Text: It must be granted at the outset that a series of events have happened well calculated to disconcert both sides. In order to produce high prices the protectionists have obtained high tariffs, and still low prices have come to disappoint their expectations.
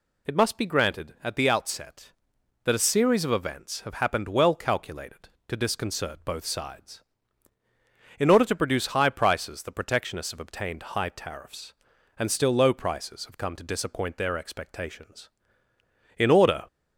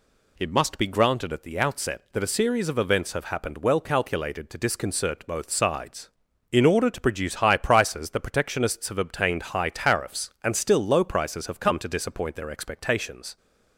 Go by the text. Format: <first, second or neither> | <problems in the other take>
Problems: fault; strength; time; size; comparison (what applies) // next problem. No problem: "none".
second | goes on to say "In order"; slight; from 16.1 s on; 0.46 s long